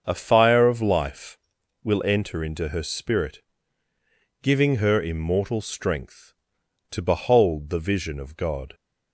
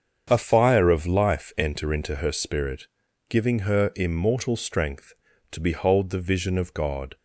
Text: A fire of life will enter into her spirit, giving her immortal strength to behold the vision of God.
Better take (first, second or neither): first